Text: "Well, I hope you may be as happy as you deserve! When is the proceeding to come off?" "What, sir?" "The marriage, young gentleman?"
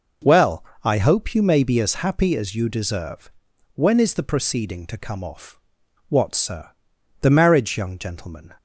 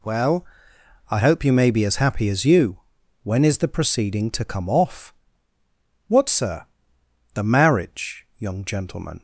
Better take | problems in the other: first | skips "deserve"; at 3.0 s

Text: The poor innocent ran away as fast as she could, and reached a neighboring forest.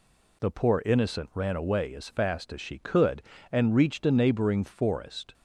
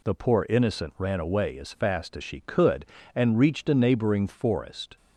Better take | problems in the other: neither | none

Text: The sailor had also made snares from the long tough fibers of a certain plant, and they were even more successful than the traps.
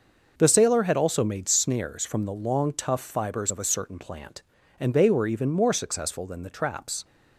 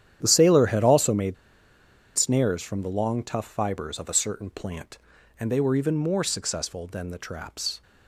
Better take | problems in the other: first | starts louder than the rest; strong; until 1.2 s; 10 dB // pauses between "made" and "snares"; noticeable; at 1.3 s; 0.80 s long

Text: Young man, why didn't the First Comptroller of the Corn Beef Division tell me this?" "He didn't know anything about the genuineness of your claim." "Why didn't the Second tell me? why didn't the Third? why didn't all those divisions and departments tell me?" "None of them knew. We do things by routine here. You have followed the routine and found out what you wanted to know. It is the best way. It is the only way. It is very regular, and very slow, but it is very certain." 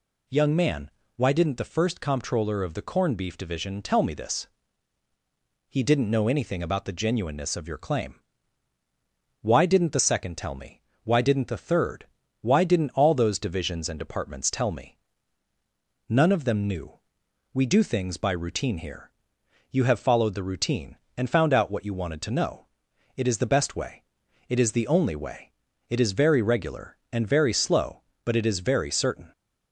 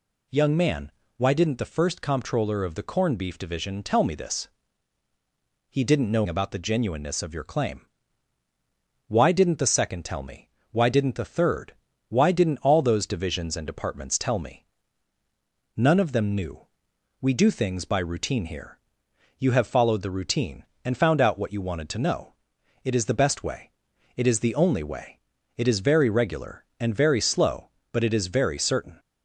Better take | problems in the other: first | skips "anything"; at 6.2 s

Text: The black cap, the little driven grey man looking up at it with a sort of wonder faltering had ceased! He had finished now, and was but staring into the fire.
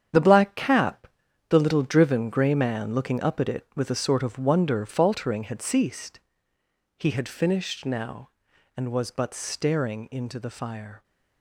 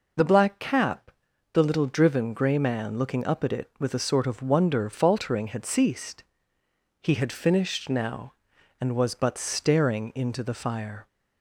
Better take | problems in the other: second | gets quieter; strong; throughout; 9.5 dB

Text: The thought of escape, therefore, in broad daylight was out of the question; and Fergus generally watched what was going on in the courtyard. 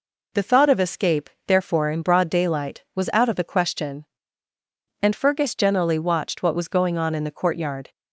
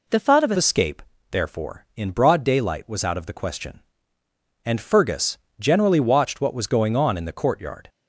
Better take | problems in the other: first | changes voice at "escape"; from 0.5 s on; 7.3 s long // pauses between "Fergus" and "generally"; slight; at 5.3 s; 0.20 s long

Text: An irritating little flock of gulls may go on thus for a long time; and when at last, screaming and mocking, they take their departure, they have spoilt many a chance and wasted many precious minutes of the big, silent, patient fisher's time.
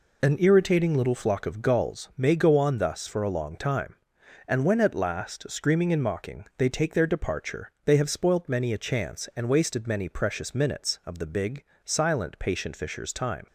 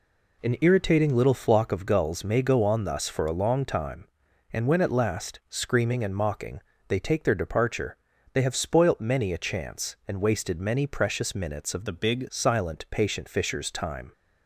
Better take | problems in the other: first | changes voice from "the" to "big"; from 11.8 to 12.2 s; 0.4 s long

